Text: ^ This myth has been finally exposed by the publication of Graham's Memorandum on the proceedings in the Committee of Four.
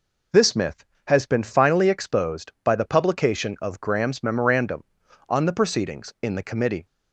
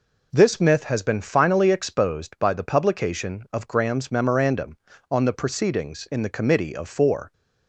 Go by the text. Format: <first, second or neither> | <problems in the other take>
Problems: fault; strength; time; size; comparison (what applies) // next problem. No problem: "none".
second | stops before "of Four"; at 6.8 s